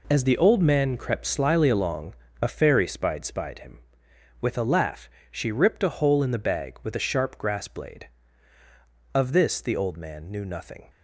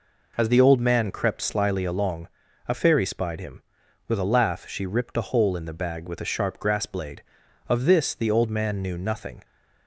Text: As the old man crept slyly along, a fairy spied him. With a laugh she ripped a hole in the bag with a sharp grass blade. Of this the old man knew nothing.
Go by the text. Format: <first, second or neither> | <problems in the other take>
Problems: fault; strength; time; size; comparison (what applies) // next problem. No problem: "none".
second | says "spied" twice; at 3.2 s // pauses between "laugh" and "she"; slight; at 5.0 s; 0.22 s long